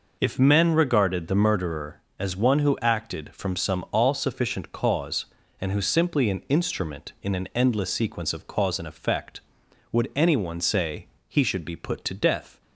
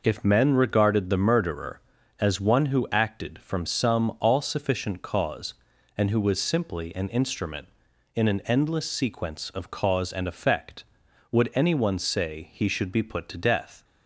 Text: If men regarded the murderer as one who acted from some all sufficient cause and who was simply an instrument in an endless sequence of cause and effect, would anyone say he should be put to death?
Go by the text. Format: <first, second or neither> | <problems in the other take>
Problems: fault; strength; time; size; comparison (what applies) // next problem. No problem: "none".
second | skips "was"; at 5.8 s // pauses between "say" and "he"; slight; at 11.0 s; 0.22 s long